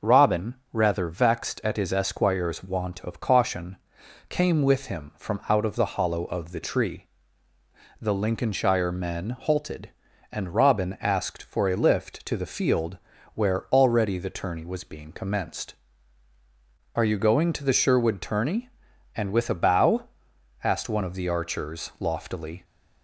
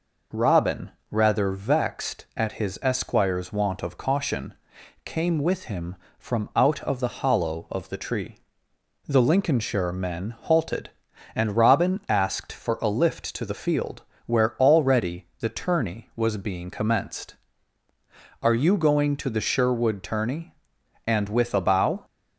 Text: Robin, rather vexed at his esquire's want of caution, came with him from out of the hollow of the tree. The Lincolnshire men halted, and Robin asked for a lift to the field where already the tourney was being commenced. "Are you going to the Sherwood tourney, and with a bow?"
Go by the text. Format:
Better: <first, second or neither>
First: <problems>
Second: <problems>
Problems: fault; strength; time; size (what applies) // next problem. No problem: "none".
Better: second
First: pauses between "field" and "where"; slight; at 12.9 s; 0.36 s long // goes on to say "asked one of the archers loftily"; strong; from 20.6 s on; 1.9 s long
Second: pauses between "field" and "where"; slight; at 14.0 s; 0.22 s long